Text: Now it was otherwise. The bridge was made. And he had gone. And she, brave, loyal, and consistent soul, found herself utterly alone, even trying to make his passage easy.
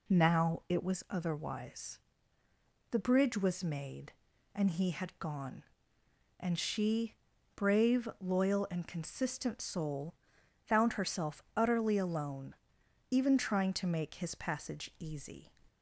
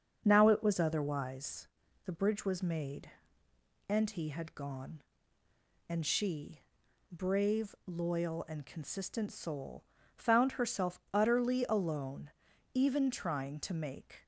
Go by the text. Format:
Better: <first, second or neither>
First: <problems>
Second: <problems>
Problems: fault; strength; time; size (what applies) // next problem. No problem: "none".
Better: first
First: none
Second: starts louder than the rest; until 1.2 s; 6.5 dB // stops before "his passage easy"; at 14.2 s